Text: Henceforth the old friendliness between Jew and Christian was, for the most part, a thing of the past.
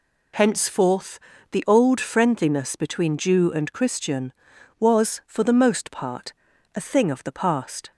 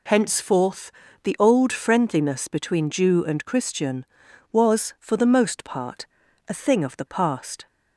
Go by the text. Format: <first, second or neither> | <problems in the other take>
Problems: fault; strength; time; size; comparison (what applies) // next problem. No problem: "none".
neither | pauses between "Henceforth" and "the"; slight; the same in both